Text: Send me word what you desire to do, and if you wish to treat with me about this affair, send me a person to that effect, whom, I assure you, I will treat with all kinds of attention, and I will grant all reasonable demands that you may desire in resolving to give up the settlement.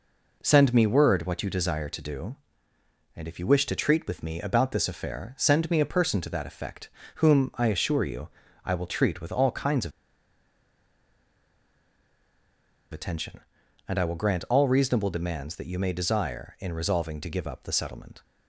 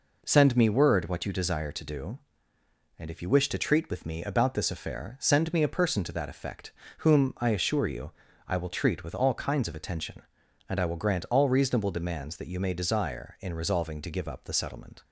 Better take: second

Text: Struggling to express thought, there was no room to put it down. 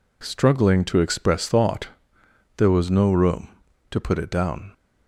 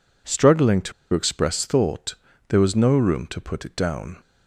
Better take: first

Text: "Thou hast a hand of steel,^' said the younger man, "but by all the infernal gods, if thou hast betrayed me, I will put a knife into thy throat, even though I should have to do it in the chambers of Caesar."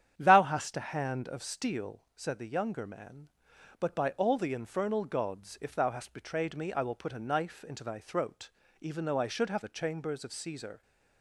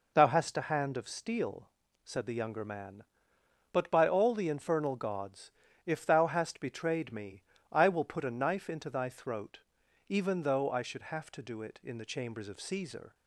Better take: second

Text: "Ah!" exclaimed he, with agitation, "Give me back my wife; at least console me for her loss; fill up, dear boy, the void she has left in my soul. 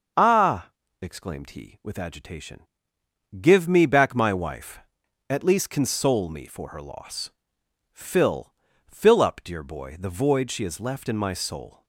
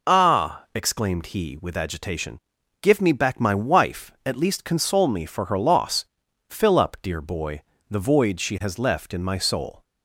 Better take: second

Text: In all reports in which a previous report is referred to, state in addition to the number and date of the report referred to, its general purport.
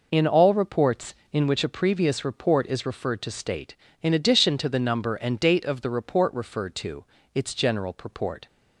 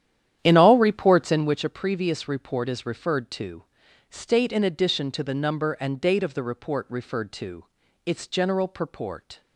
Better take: first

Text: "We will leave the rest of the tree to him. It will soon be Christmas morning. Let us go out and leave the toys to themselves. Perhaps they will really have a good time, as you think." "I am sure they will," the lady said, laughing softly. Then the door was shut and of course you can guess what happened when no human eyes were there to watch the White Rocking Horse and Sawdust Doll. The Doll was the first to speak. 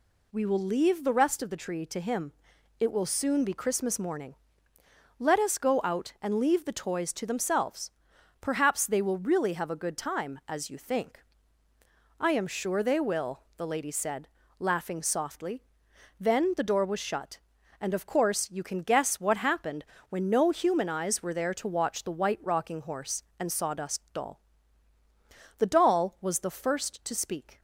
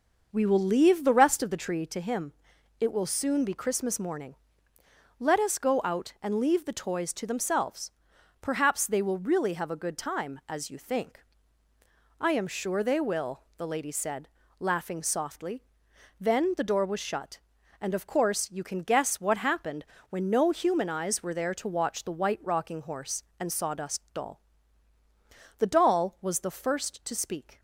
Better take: first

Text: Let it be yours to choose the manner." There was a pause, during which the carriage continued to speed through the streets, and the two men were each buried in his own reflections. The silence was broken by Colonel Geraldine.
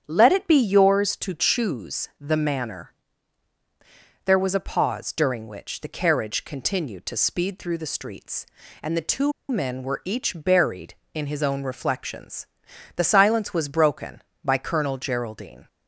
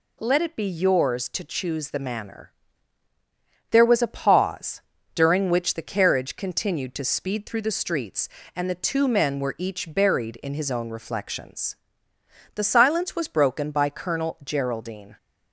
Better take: second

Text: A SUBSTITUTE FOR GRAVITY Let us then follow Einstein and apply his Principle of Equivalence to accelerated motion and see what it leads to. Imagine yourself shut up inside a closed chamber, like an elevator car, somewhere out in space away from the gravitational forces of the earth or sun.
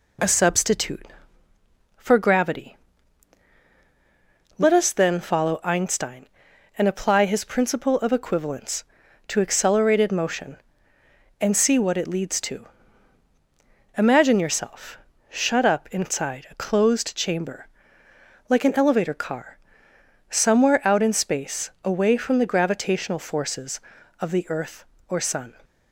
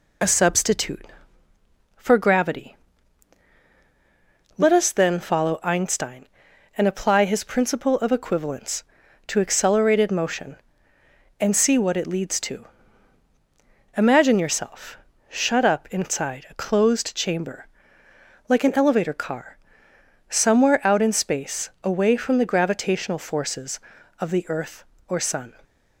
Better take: first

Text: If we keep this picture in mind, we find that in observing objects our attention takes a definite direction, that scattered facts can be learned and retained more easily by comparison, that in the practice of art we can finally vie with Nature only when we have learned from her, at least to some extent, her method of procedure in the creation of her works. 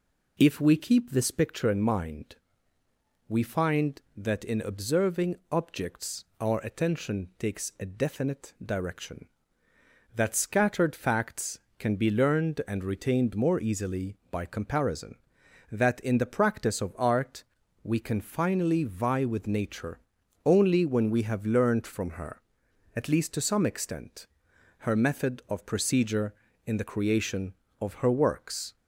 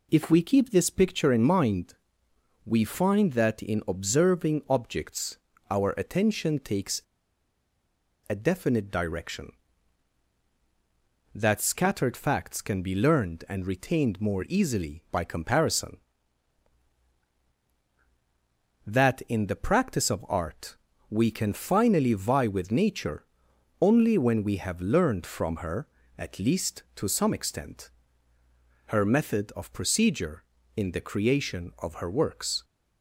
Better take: first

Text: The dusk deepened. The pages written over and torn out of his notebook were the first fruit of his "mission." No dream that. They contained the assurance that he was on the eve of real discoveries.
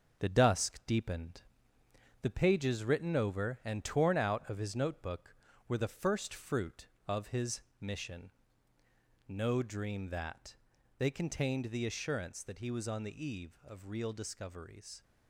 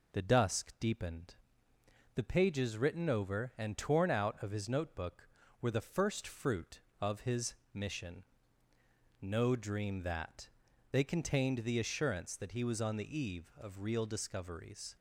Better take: second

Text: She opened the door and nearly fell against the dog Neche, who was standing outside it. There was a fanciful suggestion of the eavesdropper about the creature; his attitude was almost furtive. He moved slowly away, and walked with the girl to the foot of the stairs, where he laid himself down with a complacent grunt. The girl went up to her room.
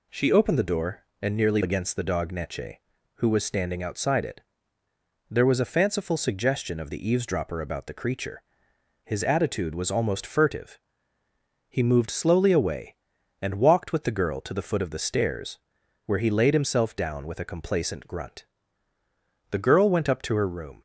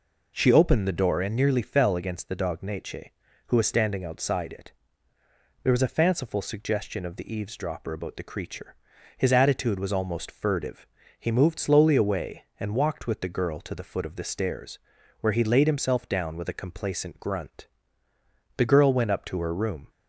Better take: second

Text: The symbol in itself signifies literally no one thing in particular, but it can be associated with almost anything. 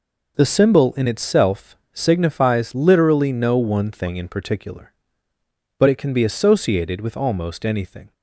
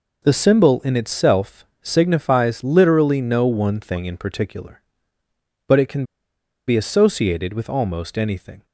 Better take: first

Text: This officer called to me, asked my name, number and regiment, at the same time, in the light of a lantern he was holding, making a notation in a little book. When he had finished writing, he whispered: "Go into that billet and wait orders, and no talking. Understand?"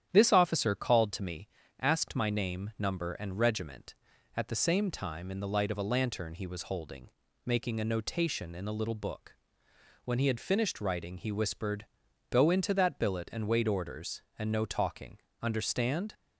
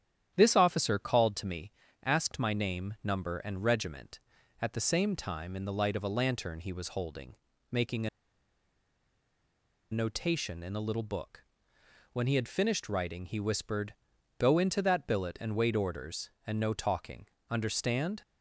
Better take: first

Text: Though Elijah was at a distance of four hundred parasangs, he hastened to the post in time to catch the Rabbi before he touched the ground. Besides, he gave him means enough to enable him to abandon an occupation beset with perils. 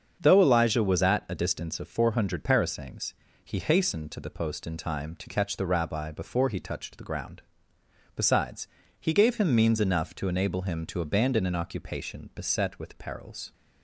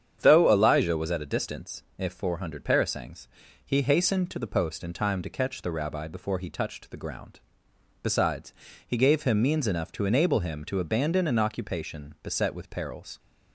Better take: first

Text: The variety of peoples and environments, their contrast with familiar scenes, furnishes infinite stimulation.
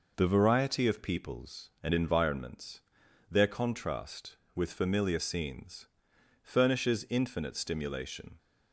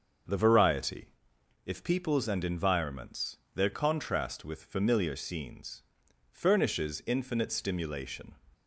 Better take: first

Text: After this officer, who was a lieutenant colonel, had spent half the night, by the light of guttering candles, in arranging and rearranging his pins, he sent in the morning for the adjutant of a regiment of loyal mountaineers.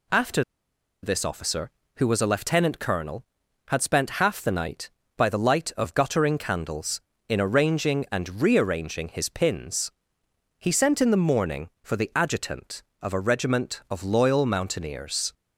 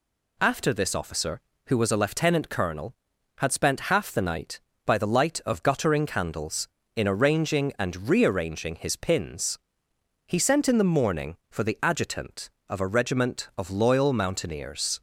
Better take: second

